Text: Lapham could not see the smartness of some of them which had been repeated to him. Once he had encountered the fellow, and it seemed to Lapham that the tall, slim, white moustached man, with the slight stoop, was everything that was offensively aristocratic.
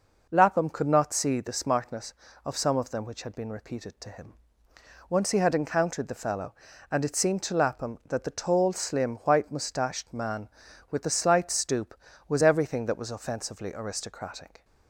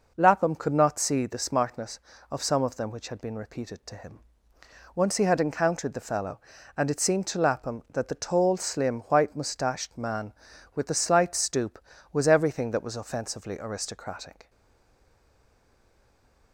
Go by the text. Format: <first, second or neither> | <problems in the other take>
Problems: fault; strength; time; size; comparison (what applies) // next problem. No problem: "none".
first | stays silent after the last word; noticeable; from 14.4 s on; 2.1 s long